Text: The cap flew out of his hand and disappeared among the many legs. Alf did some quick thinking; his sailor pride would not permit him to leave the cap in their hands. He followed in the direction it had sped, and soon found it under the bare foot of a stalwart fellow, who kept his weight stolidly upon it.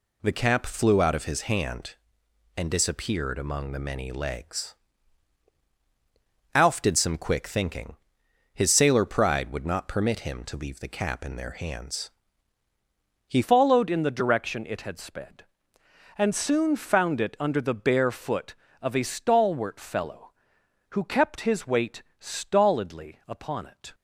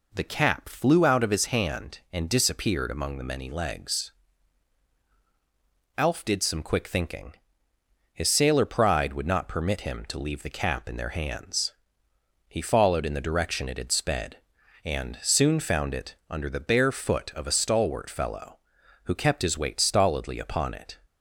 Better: second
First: changes voice at "followed"; from 13.4 s on; 10.5 s long // pauses between "weight" and "stolidly"; slight; at 22.0 s; 0.16 s long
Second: none

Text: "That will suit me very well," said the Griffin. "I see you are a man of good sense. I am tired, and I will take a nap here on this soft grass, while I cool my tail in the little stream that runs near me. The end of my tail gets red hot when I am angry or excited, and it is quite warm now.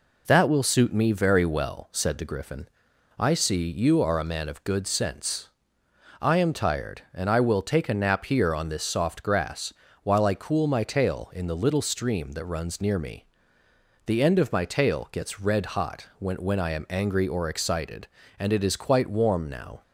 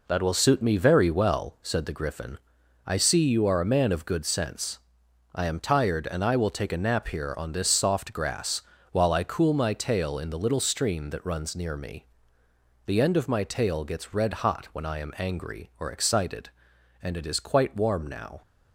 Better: second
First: says "when" twice; at 16.3 s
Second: none

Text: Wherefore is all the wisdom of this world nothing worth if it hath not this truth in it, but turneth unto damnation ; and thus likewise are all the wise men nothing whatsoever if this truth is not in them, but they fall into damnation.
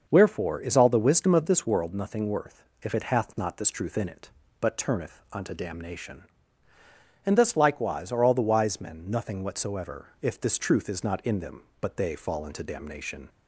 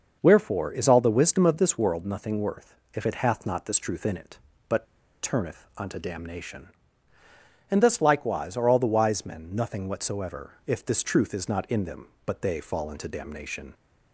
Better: first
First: pauses between "worth" and "if"; slight; at 2.6 s; 0.18 s long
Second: starts louder than the rest; noticeable; until 1.2 s; 6 dB // pauses between "worth" and "if"; slight; at 2.7 s; 0.18 s long // pauses between "but" and "turneth"; at 4.8 s; 0.37 s long

